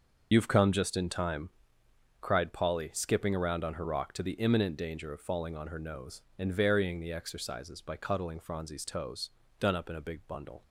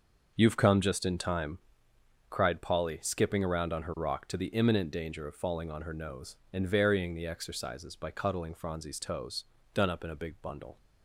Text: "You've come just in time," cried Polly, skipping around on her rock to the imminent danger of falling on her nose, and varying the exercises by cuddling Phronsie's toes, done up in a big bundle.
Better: second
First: loses the start of "You've"; at 0.3 s; 50 ms // starts louder than the rest; noticeable; until 1.3 s; 6 dB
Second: starts louder than the rest; until 1.3 s; 6 dB

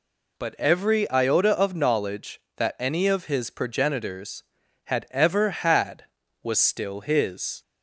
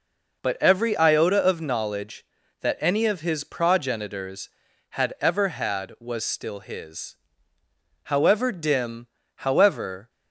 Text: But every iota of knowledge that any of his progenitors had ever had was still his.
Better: first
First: none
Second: goes on to say "However dim however"; strong; from 8.0 s on; 2.0 s long

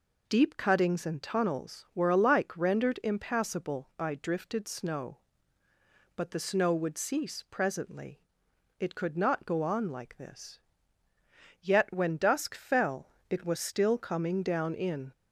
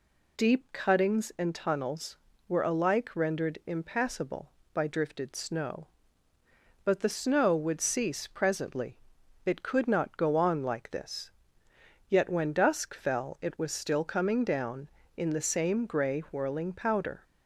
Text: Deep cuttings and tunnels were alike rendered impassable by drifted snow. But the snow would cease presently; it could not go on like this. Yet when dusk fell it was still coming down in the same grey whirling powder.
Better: second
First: pauses between "fell" and "it"; slight; at 13.0 s; 0.20 s long // stops before "the same grey whirling powder"; at 15.1 s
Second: none

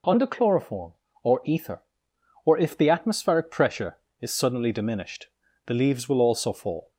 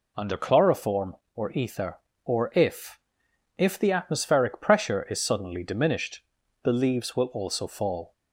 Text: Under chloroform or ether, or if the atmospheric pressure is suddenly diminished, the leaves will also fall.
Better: first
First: none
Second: says "if" twice; at 3.5 s

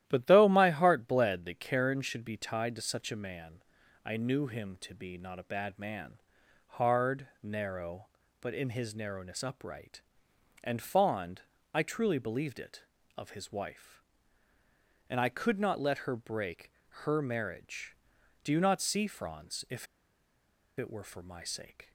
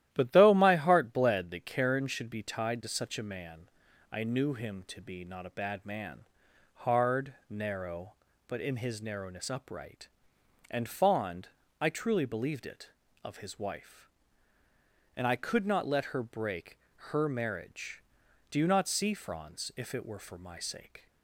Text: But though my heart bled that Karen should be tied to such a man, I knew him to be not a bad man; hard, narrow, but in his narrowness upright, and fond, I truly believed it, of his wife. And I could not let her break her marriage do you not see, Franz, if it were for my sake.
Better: second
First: starts louder than the rest; strong; until 1.0 s; 13 dB // pauses between "break" and "her"; slight; at 16.6 s; 0.34 s long // pauses between "if" and "it"; noticeable; at 19.8 s; 0.92 s long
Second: starts louder than the rest; strong; until 1.1 s; 13 dB // pauses between "break" and "her"; slight; at 16.7 s; 0.34 s long

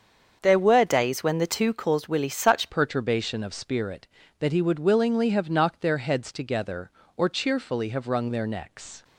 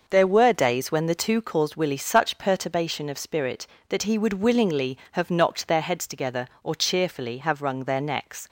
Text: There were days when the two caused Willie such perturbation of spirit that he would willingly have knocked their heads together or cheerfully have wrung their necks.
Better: second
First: starts louder than the rest; until 1.4 s; 7 dB // changes voice at "perturbation"; from 2.6 s on; 6.4 s long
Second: none

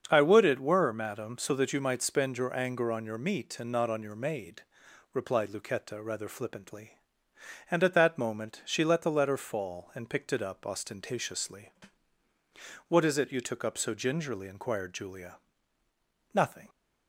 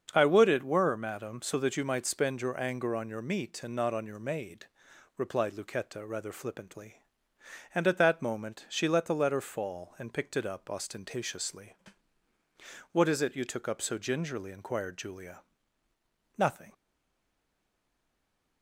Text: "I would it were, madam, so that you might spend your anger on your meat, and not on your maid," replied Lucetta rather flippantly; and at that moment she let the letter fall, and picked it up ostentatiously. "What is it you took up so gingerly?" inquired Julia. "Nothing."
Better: first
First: starts louder than the rest; until 1.1 s; 7 dB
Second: starts louder than the rest; until 1.1 s; 7 dB // stays silent after the last word; noticeable; from 16.7 s on; 1.9 s long

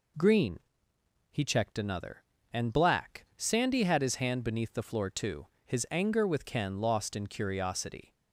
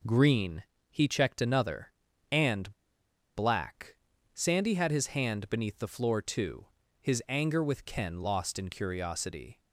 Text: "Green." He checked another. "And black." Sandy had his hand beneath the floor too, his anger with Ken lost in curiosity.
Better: first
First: none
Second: pauses between "And" and "black"; noticeable; at 2.7 s; 0.61 s long

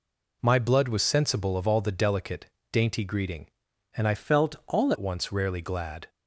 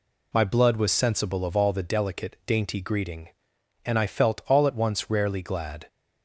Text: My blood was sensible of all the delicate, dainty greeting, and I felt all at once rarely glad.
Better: second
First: changes voice from "felt" to "all"; from 4.1 to 4.9 s; 0.8 s long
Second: none

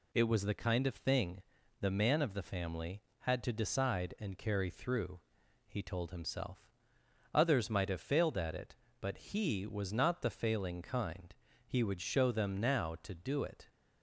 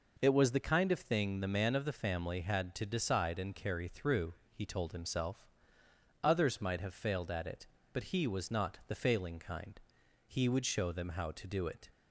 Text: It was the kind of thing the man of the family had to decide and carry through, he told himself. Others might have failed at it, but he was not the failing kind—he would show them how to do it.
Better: second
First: pauses between "thing" and "the"; at 1.4 s; 0.38 s long // says "now" for "how"; at 12.5 s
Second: none

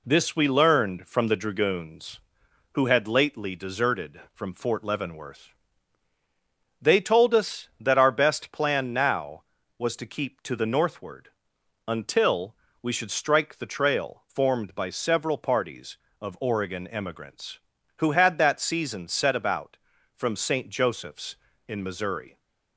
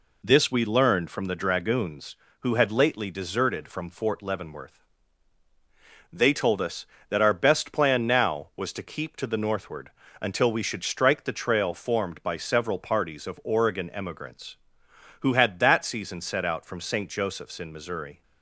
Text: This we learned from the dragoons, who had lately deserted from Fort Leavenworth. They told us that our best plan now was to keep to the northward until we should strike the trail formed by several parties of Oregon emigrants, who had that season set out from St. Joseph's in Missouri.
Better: second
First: pauses between "northward" and "until"; noticeable; at 11.2 s; 0.58 s long // pauses between "until" and "we"; slight; at 12.5 s; 0.26 s long // says "about" for "out"; at 19.3 s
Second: pauses between "northward" and "until"; slight; at 9.9 s; 0.30 s long

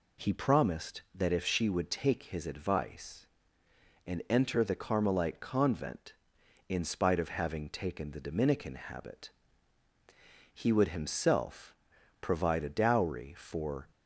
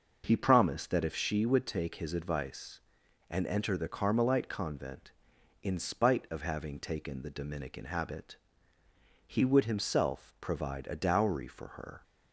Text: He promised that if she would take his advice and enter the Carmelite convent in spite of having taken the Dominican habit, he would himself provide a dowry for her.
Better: second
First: pauses between "himself" and "provide"; noticeable; at 11.7 s; 0.48 s long // stops before "her"; at 13.9 s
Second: none

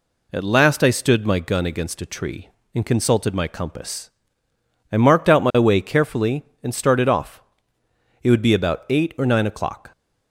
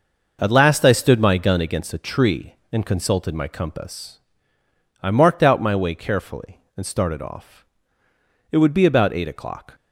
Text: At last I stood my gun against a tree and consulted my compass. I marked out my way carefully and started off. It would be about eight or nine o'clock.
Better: first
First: none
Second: skips "or nine"; at 9.2 s

